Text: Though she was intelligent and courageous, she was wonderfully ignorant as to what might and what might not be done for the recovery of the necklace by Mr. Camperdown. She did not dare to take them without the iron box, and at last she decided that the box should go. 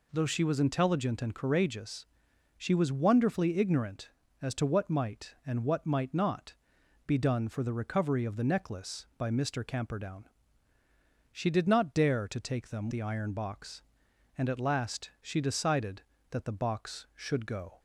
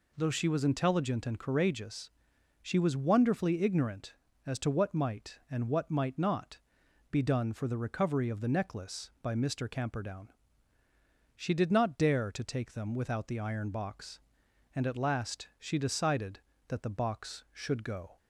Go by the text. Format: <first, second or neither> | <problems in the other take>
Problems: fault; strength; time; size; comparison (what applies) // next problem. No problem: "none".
second | pauses between "not" and "be"; noticeable; at 6.5 s; 0.50 s long; noticeable in the second // skips "without"; at 12.8 s